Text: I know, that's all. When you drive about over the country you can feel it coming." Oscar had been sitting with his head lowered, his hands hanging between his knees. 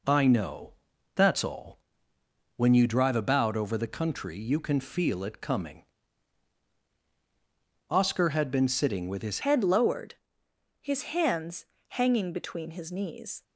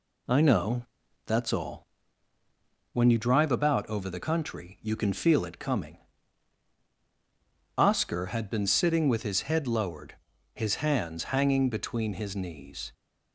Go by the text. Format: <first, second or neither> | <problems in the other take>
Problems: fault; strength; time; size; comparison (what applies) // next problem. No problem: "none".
second | changes voice at "head"; from 9.4 s on; 4.0 s long // pauses between "hands" and "hanging"; slight; at 11.6 s; 0.24 s long